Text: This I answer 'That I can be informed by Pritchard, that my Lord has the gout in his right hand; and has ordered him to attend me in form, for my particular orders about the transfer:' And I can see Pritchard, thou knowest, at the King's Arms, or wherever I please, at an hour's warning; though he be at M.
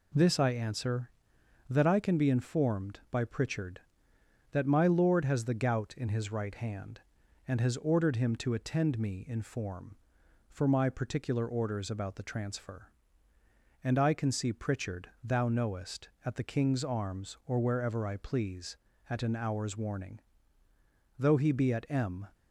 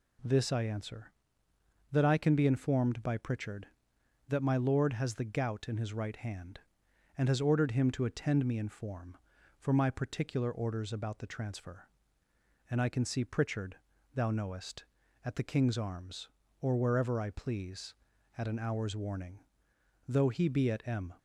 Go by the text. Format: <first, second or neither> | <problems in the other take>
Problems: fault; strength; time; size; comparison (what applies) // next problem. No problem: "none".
neither | none